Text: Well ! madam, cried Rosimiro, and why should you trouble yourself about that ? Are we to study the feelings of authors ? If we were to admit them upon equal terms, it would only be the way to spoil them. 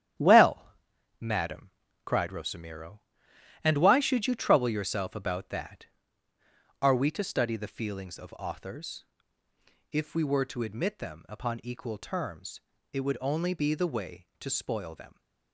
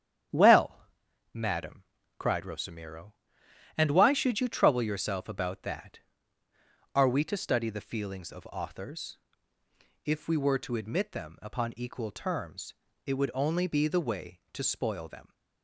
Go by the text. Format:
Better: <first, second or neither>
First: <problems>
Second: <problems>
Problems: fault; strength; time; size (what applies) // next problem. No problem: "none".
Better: second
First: gets quieter; throughout; 7 dB // starts louder than the rest; strong; until 1.6 s; 10.5 dB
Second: starts louder than the rest; strong; until 1.8 s; 9.5 dB